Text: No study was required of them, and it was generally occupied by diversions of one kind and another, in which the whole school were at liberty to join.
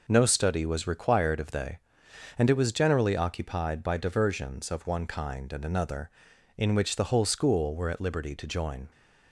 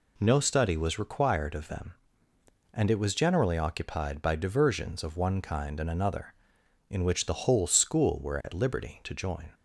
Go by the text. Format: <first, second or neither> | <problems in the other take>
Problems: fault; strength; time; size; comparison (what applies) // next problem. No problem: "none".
second | says "they" for "them"; at 1.5 s